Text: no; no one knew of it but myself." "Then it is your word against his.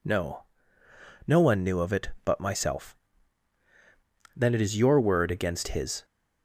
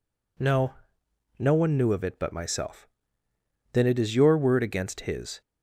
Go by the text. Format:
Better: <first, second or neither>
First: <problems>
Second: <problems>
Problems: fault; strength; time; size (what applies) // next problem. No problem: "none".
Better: neither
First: none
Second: none